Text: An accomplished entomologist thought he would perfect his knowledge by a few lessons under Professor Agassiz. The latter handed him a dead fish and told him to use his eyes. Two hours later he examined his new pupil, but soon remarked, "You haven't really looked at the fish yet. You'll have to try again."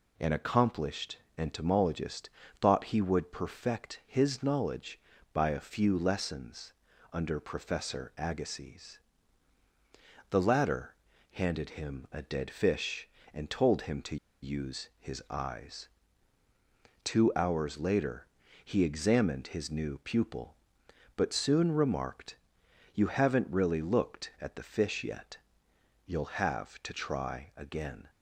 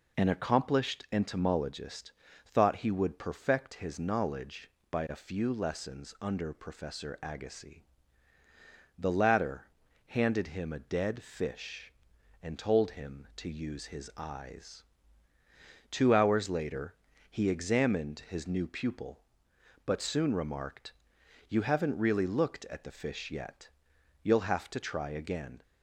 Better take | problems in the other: second | pauses between "accomplished" and "entomologist"; slight; at 1.1 s; 0.20 s long // pauses between "entomologist" and "thought"; slight; at 2.2 s; 0.32 s long; slight in the second // pauses between "lessons" and "under"; at 6.7 s; 0.40 s long // pauses between "latter" and "handed"; at 10.9 s; 0.38 s long; also in the second // pauses between "to" and "use"; slight; at 14.1 s; 0.26 s long // pauses between "later" and "he"; at 18.2 s; 0.38 s long; slight in the second

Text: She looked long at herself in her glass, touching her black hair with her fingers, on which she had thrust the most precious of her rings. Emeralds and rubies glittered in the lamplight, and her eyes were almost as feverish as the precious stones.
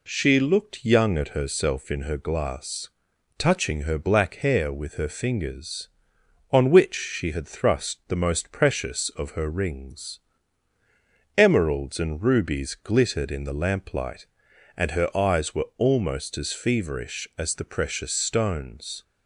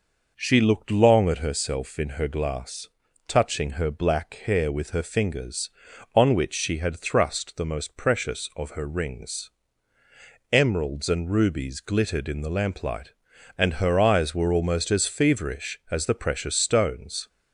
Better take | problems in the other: second | says "young" for "long"; at 0.8 s

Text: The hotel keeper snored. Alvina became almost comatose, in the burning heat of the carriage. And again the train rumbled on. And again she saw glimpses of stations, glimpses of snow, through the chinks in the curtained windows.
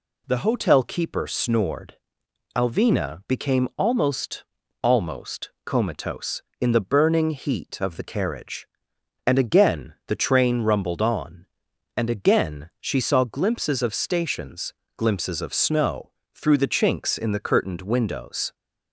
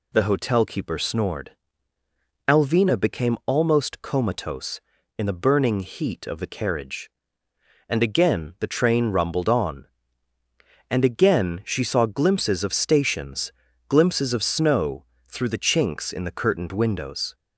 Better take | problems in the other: second | says "almost" twice; at 4.8 s

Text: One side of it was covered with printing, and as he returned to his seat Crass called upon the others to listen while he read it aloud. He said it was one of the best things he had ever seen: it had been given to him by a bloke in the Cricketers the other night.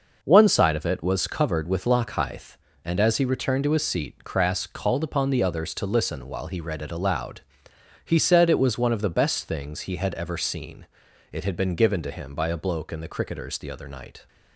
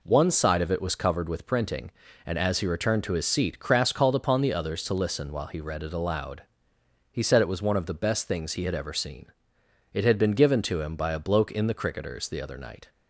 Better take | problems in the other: second | says "lockhithe" for "printing"; at 1.8 s

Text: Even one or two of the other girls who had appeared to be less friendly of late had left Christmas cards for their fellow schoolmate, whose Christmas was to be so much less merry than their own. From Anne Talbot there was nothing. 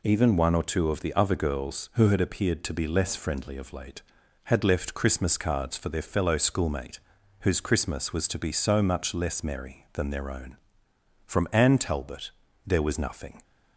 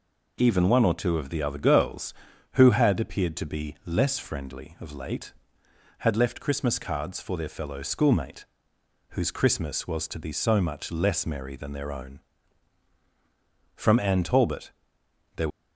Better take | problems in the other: first | pauses between "Talbot" and "there"; noticeable; at 14.7 s; 0.64 s long; slight in the first // stops before "was nothing"; at 15.5 s

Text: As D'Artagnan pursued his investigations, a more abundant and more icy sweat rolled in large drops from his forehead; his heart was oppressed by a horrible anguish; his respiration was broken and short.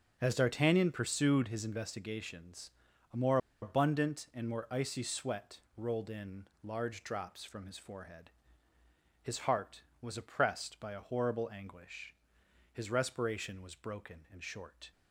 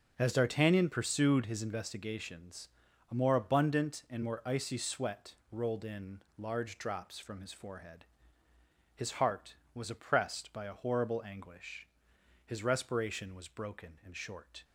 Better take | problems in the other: second | starts louder than the rest; strong; until 1.2 s; 7 dB; also in the second // pauses between "more" and "abundant"; slight; at 3.3 s; 0.24 s long // pauses between "sweat" and "rolled"; slight; at 5.5 s; 0.16 s long; slight in the second // pauses between "in" and "large"; slight; at 6.4 s; 0.16 s long; slight in the second

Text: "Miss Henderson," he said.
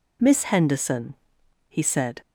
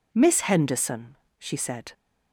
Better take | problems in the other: first | says "she" for "he"; at 1.3 s

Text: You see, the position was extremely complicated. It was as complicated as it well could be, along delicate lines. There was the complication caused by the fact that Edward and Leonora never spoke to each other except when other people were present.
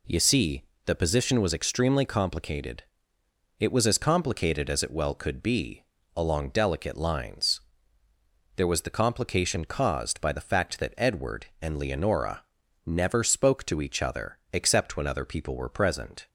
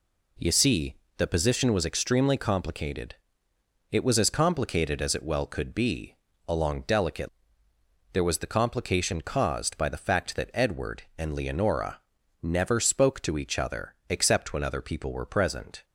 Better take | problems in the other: first | skips "lines"; at 7.7 s // pauses between "Leonora" and "never"; at 12.0 s; 0.42 s long; also in the first

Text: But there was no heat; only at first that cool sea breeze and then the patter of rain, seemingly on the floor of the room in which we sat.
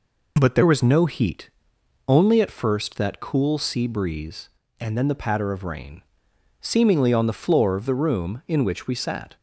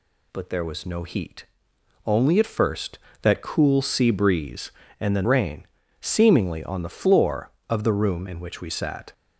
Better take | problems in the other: first | skips "the patter of"; at 5.2 s

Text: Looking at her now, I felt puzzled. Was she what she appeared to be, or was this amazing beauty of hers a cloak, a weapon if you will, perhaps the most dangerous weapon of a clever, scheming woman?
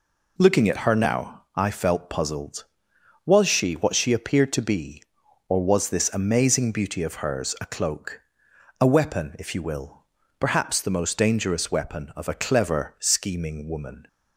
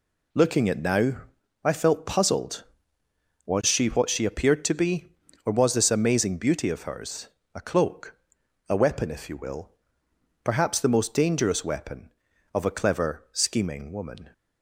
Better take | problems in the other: first | skips "her"; at 0.7 s // pauses between "hers" and "a"; slight; at 7.2 s; 0.26 s long

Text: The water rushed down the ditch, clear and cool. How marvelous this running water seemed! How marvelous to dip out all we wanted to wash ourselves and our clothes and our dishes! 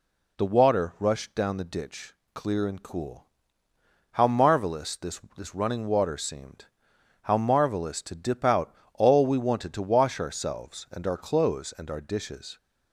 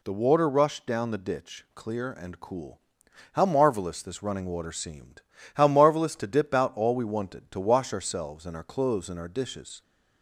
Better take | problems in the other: second | says "this" twice; at 5.3 s // pauses between "out" and "all"; slight; at 8.7 s; 0.22 s long

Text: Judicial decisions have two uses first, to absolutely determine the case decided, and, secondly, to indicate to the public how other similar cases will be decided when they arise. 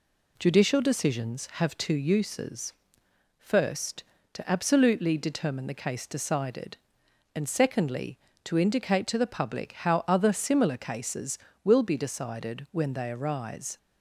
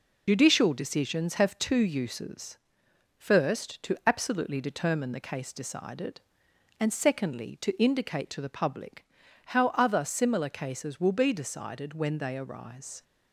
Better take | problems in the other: first | loses the start of "Judicial"; at 0.2 s; 45 ms // pauses between "uses" and "first"; noticeable; at 2.5 s; 0.60 s long; noticeable in the first // pauses between "public" and "how"; at 9.0 s; 0.42 s long

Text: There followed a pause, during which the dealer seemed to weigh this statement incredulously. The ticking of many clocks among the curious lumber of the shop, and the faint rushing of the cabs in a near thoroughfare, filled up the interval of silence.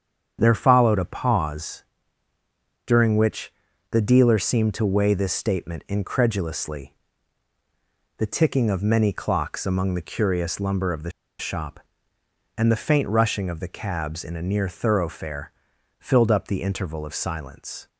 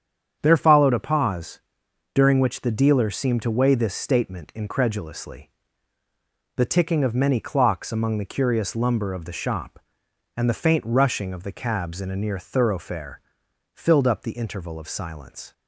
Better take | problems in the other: second | starts louder than the rest; strong; until 1.4 s; 8 dB; strong in the second // pauses between "which" and "the"; at 3.5 s; 0.38 s long // pauses between "the" and "shop"; slight; at 11.0 s; 0.29 s long

